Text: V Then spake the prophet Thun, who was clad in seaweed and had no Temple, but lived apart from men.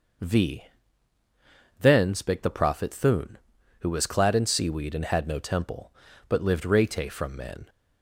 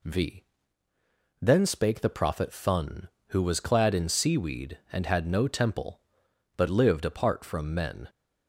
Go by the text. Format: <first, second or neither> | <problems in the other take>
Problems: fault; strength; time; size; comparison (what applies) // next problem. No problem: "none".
second | pauses between "V" and "Then"; at 0.6 s; 1.1 s long; noticeable in the second // says "rete" for "apart"; at 6.6 s